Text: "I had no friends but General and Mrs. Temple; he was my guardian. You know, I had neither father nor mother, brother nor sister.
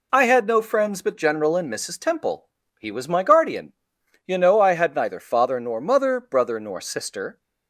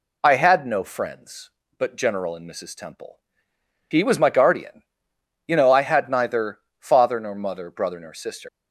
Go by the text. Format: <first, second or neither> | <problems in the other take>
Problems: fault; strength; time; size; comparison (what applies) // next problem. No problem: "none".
first | pauses between "neither" and "father"; slight; at 6.5 s; 0.22 s long // leaves "sister" unfinished; at 8.4 s; 150 ms